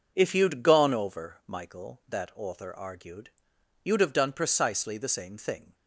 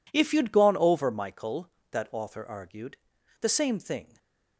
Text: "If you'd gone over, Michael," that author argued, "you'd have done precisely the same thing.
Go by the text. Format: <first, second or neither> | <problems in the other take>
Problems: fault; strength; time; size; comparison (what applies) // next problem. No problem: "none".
first | skips "you'd have done precisely"; at 3.1 s // stays silent after the last word; slight; from 4.0 s on; 0.5 s long